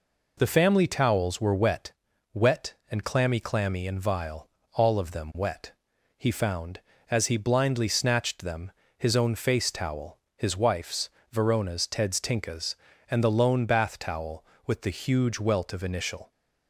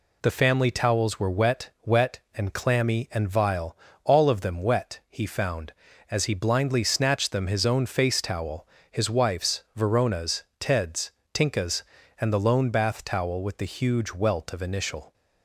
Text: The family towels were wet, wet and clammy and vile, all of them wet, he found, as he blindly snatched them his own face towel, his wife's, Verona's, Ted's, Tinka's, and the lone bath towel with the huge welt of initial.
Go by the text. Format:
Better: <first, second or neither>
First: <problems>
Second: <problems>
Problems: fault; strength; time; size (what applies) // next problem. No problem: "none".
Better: second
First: says "clammy" twice; at 3.4 s // pauses between "them" and "his"; slight; at 8.7 s; 0.26 s long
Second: none